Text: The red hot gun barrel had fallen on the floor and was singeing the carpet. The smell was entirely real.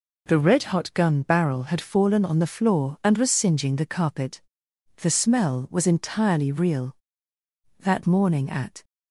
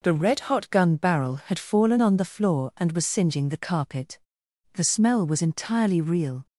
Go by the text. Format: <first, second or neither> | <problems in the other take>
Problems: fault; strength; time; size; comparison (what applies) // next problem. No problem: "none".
second | goes on to say "That morning at"; noticeable; from 7.8 s on; 1.0 s long